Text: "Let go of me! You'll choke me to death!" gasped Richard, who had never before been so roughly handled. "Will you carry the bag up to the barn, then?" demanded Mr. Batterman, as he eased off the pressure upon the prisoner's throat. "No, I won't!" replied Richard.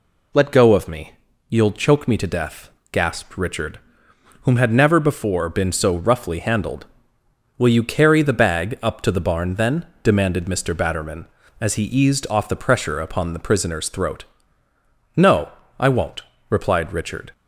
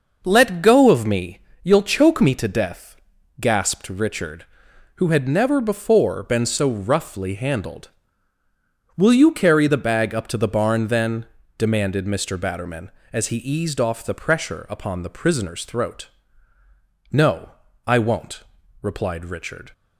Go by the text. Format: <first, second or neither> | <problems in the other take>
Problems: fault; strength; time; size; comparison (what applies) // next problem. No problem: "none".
second | says "whom" for "who"; at 4.4 s